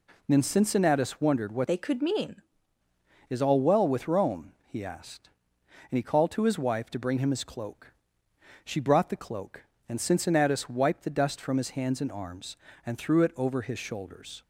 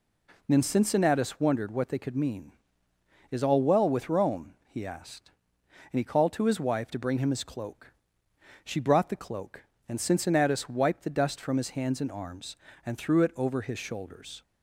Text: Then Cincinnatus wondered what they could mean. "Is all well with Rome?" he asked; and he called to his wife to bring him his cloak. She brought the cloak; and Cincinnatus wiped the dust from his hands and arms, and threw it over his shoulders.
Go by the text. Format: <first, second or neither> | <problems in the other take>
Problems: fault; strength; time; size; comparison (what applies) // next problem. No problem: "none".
second | changes voice from "they" to "mean"; from 1.6 to 2.4 s; 0.8 s long